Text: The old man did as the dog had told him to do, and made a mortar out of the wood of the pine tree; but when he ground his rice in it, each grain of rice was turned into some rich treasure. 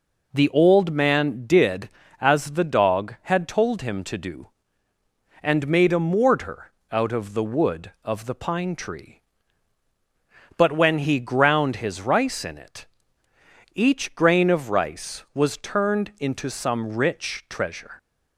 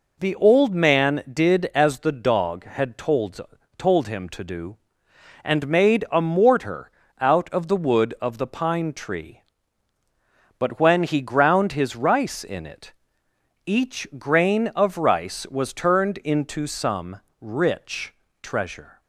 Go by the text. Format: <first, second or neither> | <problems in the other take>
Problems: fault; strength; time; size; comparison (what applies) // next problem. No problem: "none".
first | says "told" twice; at 3.7 s // pauses between "mortar" and "out"; slight; at 6.8 s; 0.30 s long; slight in the first // pauses between "some" and "rich"; slight; at 17.1 s; 0.22 s long // pauses between "rich" and "treasure"; slight; at 18.1 s; 0.28 s long